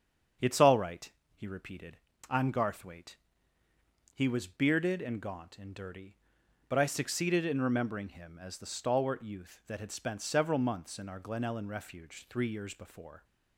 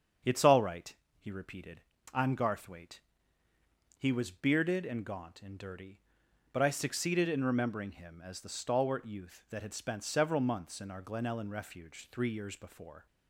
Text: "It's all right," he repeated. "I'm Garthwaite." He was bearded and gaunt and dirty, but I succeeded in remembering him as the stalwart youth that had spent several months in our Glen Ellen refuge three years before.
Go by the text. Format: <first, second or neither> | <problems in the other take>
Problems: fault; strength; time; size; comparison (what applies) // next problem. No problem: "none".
neither | starts louder than the rest; strong; the same in both